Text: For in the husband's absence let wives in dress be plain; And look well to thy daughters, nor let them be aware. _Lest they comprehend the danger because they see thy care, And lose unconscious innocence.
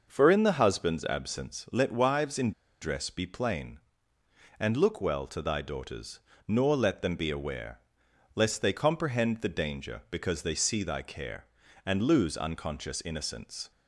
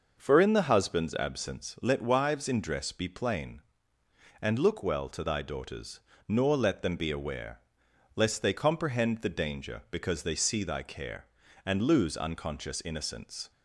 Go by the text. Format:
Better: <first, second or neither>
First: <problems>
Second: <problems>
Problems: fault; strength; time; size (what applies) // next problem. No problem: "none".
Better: second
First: pauses between "in" and "dress"; slight; at 2.5 s; 0.30 s long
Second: none